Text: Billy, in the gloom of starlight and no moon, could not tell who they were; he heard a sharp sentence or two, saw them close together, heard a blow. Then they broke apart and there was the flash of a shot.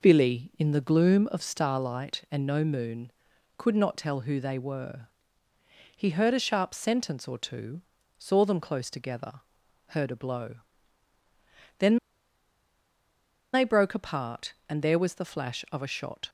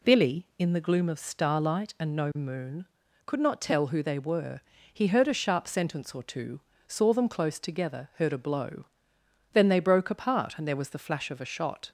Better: second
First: pauses between "Then" and "they"; strong; at 11.9 s; 1.5 s long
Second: none

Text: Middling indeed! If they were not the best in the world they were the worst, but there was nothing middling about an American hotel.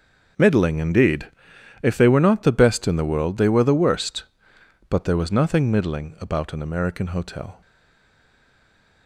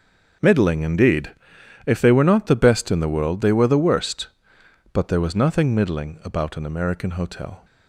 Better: second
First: stays silent after the last word; noticeable; from 7.6 s on; 1.4 s long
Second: none

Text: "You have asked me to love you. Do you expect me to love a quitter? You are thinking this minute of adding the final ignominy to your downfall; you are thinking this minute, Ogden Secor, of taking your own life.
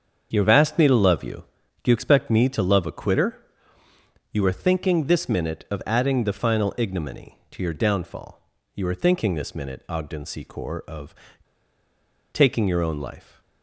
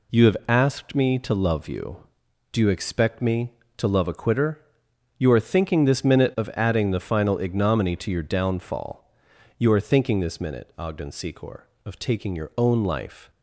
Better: second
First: starts louder than the rest; until 1.3 s; 7 dB // pauses between "of" and "taking"; at 11.1 s; 1.1 s long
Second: none

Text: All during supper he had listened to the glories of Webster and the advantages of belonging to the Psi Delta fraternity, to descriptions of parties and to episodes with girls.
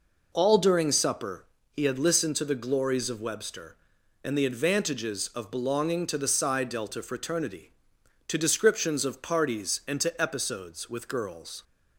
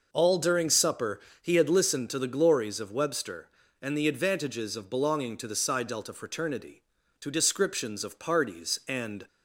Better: first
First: pauses between "supper" and "he"; slight; at 1.4 s; 0.30 s long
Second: pauses between "supper" and "he"; slight; at 1.2 s; 0.20 s long // stops before "to episodes with girls"; at 9.2 s

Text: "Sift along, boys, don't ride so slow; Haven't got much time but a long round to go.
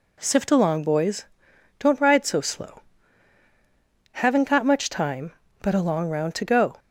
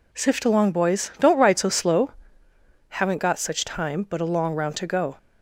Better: first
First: none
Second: says "such" for "much"; at 3.3 s

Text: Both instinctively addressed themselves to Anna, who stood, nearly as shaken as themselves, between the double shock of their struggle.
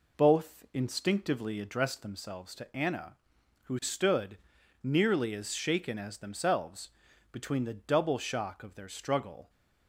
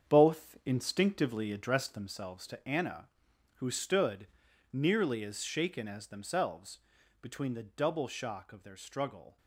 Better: first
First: none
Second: gets quieter; strong; throughout; 8.5 dB

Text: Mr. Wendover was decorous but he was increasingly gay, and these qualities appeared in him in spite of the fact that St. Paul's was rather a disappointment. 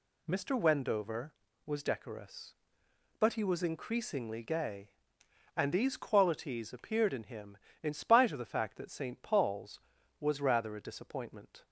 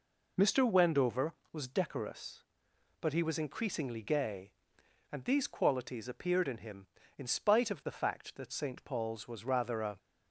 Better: first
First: none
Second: stops before "disappointment"; at 9.9 s

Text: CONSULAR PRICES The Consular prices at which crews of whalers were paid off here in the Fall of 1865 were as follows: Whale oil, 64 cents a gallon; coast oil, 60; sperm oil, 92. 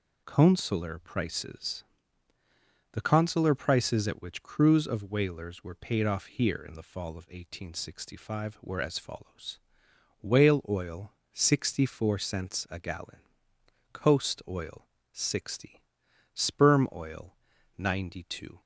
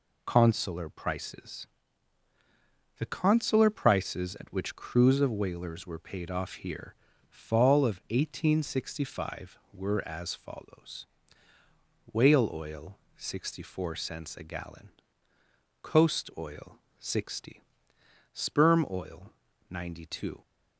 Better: first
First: pauses between "PRICES" and "The"; at 1.8 s; 1.0 s long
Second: pauses between "PRICES" and "The"; strong; at 1.6 s; 1.3 s long // skips "in the"; at 7.1 s

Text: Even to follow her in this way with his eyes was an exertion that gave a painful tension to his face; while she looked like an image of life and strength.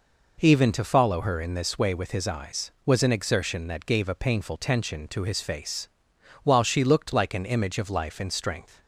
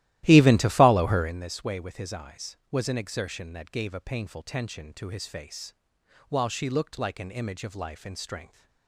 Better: first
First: none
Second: starts louder than the rest; strong; until 1.4 s; 15 dB

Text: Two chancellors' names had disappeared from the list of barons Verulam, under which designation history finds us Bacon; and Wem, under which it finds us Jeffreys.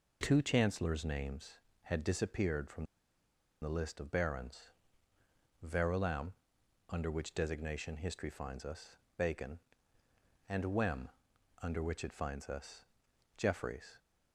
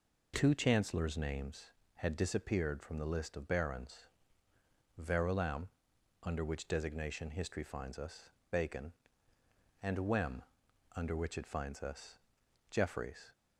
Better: second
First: pauses between "from" and "the"; noticeable; at 2.8 s; 0.76 s long // pauses between "barons" and "Verulam"; noticeable; at 4.7 s; 0.92 s long // pauses between "us" and "Bacon"; slight; at 8.9 s; 0.20 s long // pauses between "us" and "Jeffreys"; noticeable; at 12.8 s; 0.52 s long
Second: pauses between "barons" and "Verulam"; noticeable; at 4.0 s; 0.90 s long // pauses between "us" and "Bacon"; slight; at 8.2 s; 0.20 s long // pauses between "us" and "Jeffreys"; noticeable; at 12.1 s; 0.52 s long

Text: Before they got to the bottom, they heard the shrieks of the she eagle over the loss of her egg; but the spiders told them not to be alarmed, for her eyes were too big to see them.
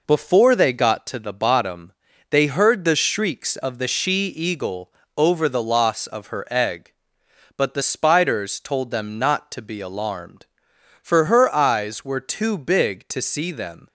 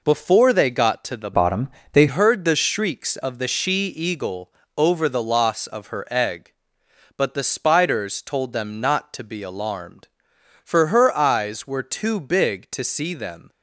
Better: first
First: pauses between "eagle" and "over"; slight; at 4.9 s; 0.26 s long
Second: changes voice from "bottom" to "they"; from 1.3 to 2.0 s; 0.7 s long // pauses between "eagle" and "over"; slight; at 4.5 s; 0.26 s long

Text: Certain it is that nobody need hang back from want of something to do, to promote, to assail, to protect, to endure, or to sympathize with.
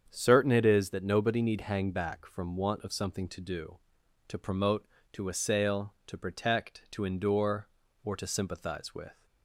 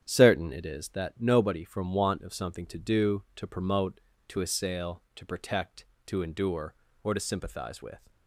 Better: first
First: starts louder than the rest; strong; until 1.1 s; 7.5 dB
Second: starts louder than the rest; strong; until 1.0 s; 9 dB // skips "need hang back"; at 1.6 s

